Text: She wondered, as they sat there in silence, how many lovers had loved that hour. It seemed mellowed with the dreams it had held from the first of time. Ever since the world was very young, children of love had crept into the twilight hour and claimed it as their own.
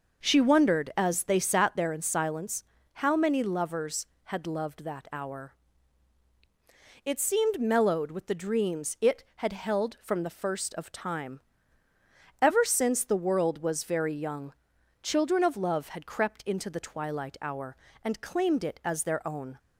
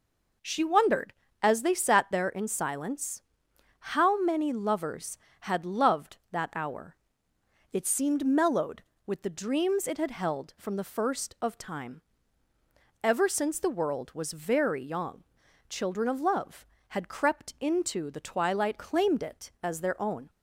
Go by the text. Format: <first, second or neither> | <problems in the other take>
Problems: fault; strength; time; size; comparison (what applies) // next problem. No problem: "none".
first | skips "hour and"; at 18.7 s